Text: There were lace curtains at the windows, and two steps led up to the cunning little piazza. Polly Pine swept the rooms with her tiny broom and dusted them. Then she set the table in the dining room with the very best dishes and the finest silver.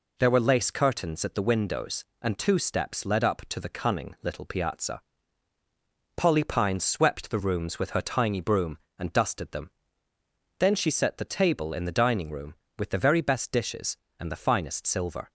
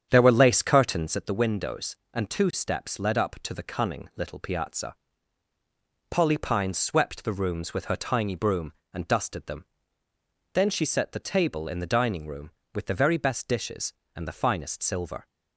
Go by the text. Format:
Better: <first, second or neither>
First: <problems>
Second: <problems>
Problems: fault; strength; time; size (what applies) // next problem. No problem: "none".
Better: first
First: none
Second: starts louder than the rest; strong; until 1.3 s; 8 dB